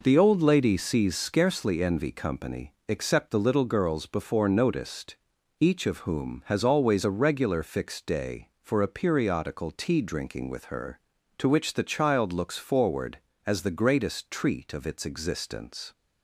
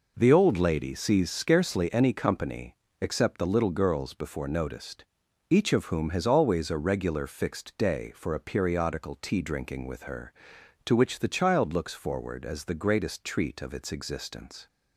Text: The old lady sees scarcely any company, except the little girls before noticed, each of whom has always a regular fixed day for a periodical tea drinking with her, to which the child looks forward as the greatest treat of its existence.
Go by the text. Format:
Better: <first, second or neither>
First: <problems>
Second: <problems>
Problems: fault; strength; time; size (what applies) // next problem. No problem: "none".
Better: second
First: says "envy" for "any"; at 1.8 s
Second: none